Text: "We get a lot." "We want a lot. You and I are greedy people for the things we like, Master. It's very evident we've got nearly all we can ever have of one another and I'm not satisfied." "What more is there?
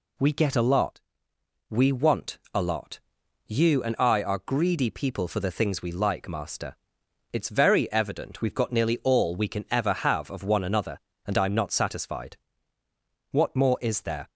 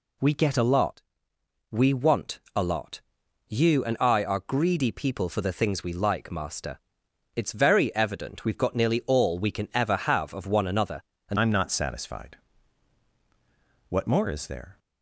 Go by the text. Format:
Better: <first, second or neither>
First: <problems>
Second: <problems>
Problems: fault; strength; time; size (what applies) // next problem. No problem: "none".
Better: first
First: pauses between "want" and "a"; slight; at 2.3 s; 0.16 s long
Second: pauses between "want" and "a"; slight; at 2.4 s; 0.16 s long // changes voice at "I'm"; from 11.3 s on; 3.4 s long